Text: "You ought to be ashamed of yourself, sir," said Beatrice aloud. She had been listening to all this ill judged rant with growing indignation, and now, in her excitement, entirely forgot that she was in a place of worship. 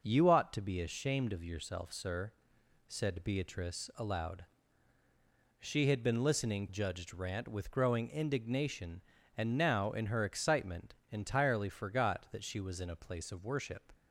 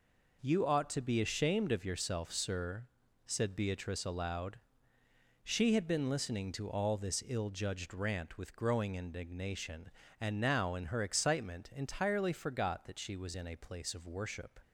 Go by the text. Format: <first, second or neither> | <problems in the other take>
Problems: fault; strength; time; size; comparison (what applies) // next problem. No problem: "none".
second | skips "to all this ill"; at 6.6 s